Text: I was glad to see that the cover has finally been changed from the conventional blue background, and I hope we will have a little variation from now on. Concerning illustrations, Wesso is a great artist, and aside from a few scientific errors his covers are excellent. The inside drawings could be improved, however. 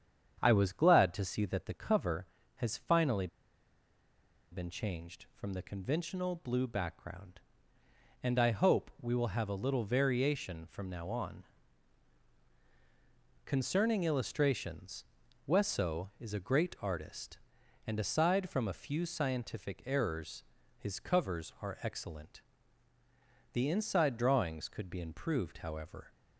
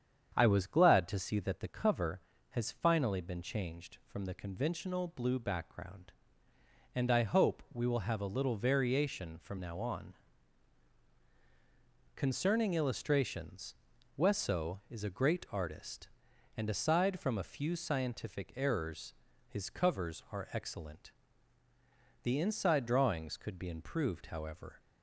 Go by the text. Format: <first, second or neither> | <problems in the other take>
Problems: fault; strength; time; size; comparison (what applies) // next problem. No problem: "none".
second | starts louder than the rest; strong; until 1.4 s; 8 dB; strong in the second // pauses between "finally" and "been"; strong; at 3.2 s; 1.2 s long // pauses between "errors" and "his"; slight; at 20.4 s; 0.36 s long; slight in the second